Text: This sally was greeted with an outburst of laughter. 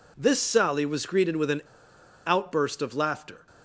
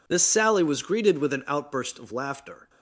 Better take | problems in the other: second | pauses between "an" and "outburst"; noticeable; at 1.6 s; 0.64 s long

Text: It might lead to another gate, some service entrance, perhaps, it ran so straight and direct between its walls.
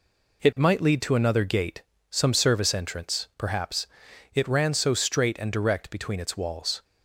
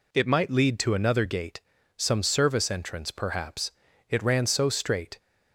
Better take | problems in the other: first | stops before "and direct between its walls"; at 5.1 s

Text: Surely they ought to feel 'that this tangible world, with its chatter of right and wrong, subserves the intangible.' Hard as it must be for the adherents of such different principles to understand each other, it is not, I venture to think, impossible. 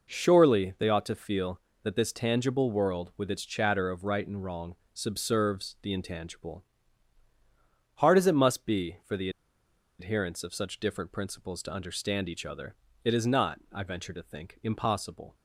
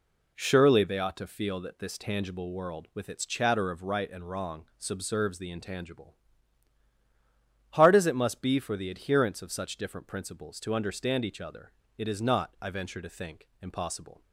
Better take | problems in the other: second | pauses between "the" and "adherents"; noticeable; at 9.2 s; 0.70 s long

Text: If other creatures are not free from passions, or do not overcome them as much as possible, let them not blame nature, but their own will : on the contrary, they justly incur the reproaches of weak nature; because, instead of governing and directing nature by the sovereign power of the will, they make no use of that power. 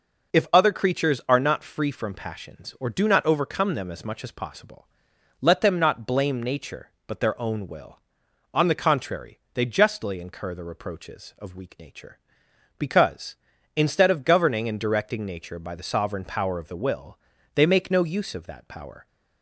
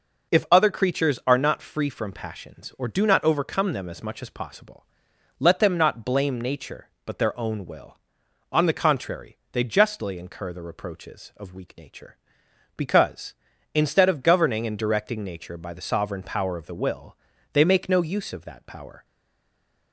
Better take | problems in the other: first | stays silent after the last word; slight; from 19.0 s on; 0.9 s long

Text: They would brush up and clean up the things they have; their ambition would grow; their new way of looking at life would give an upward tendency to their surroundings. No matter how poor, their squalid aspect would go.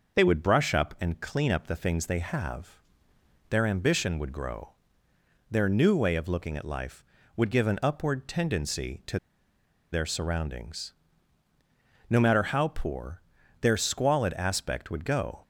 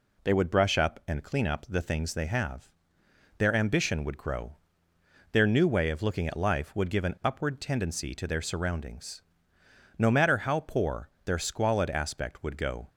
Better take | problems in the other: second | starts louder than the rest; noticeable; until 1.2 s; 6 dB // pauses between "to" and "their"; noticeable; at 9.1 s; 0.74 s long

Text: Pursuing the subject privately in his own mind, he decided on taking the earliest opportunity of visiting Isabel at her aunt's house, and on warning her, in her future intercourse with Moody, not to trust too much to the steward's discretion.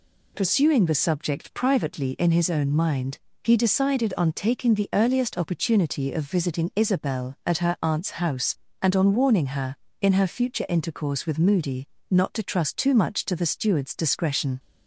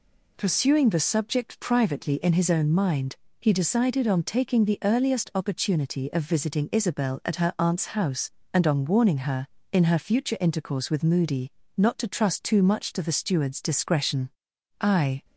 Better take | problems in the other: first | goes on to say "I"; slight; from 14.8 s on; 0.44 s long

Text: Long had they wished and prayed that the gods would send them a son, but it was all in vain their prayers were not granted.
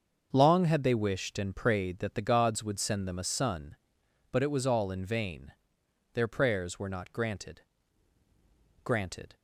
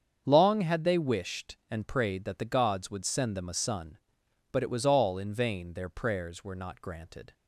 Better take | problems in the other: second | starts louder than the rest; until 1.3 s; 6.5 dB; strong in the second // pauses between "vain" and "their"; noticeable; at 5.5 s; 0.62 s long // says "granted" twice; at 8.8 s

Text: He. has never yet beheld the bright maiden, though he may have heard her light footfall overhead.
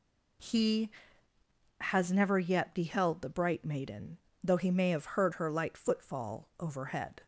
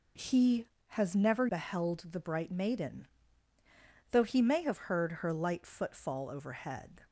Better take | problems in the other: first | skips "yet"; at 1.4 s

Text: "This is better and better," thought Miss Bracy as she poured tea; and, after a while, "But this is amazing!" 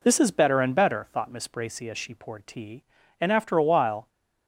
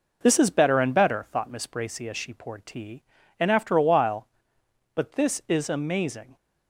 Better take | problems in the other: second | stops before "But this is amazing"; at 4.0 s

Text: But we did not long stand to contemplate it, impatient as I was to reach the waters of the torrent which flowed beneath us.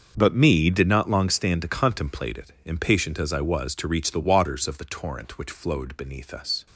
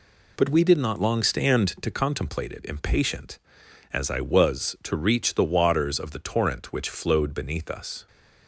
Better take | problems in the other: second | starts louder than the rest; until 1.1 s; 6.5 dB // says "me" for "we"; at 0.3 s

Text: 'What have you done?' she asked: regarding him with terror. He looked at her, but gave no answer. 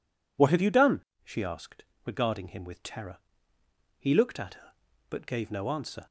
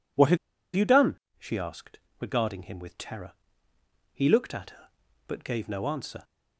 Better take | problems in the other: first | pauses between "have" and "you"; at 0.3 s; 0.37 s long

